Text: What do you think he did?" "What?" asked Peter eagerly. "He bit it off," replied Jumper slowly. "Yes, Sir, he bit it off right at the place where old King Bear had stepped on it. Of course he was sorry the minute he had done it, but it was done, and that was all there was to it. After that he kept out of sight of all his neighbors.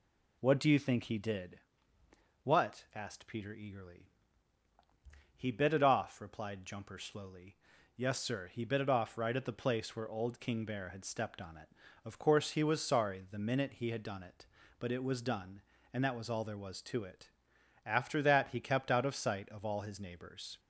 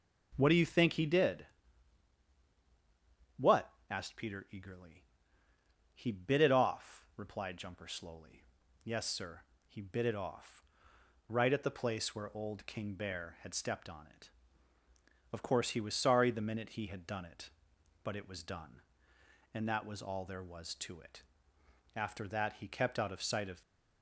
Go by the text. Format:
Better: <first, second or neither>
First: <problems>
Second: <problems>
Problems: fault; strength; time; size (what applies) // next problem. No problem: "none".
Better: first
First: none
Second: pauses between "off" and "right"; noticeable; at 10.6 s; 0.62 s long // stops before "all his neighbors"; at 23.6 s